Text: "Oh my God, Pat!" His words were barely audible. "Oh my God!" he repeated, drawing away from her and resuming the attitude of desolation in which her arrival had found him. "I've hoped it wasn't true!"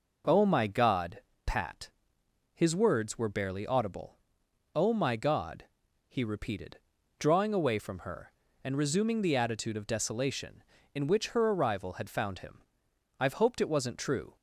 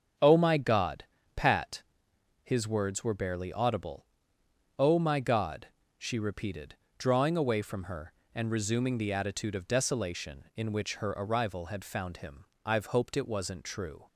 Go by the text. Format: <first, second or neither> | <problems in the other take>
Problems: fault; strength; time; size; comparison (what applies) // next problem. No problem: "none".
first | starts louder than the rest; strong; until 1.4 s; 7 dB // says "she" for "he"; at 5.9 s